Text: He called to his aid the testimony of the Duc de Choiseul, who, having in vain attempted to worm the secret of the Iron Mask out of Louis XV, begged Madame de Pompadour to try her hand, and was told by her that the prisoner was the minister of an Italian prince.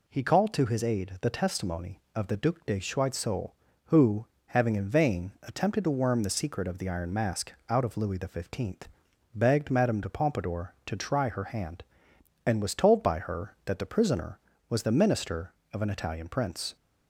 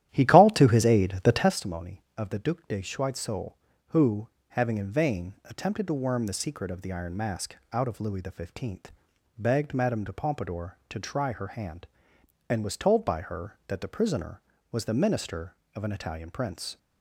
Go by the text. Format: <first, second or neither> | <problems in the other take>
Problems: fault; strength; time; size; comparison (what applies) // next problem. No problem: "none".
first | starts louder than the rest; strong; until 1.6 s; 12.5 dB // pauses between "Mask" and "out"; slight; at 7.5 s; 0.16 s long; slight in the first